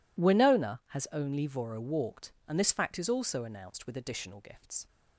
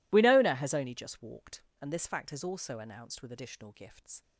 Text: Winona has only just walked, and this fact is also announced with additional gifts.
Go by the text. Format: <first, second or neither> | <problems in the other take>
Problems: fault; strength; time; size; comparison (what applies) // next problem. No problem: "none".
second | says "voro" for "just"; at 1.4 s